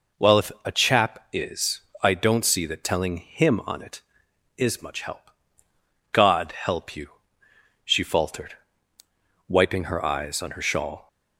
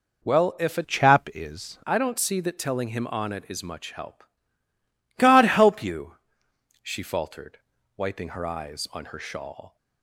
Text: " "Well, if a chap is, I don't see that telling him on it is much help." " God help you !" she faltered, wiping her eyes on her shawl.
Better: first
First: none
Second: changes voice from "chap" to "is"; from 0.8 to 1.7 s; 0.9 s long

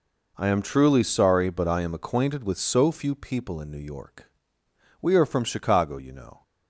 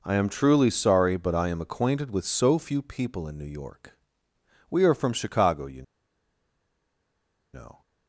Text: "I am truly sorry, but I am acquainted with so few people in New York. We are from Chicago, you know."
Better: first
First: none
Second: pauses between "you" and "know"; strong; at 5.8 s; 1.7 s long

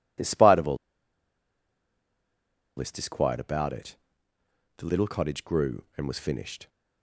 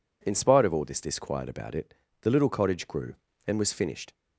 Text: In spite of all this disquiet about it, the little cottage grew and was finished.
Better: second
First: pauses between "all" and "this"; strong; at 0.7 s; 2.0 s long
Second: none

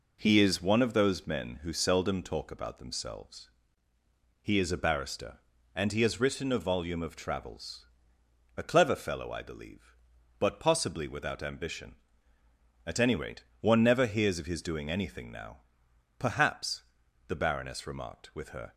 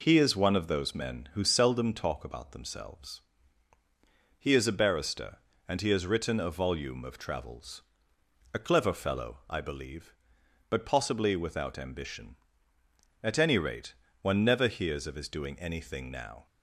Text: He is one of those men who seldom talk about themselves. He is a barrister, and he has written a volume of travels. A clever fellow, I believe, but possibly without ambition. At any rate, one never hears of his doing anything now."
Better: second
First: goes on to say "Perhaps the Baroness remarked with her"; strong; from 16.1 s on; 2.5 s long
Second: none

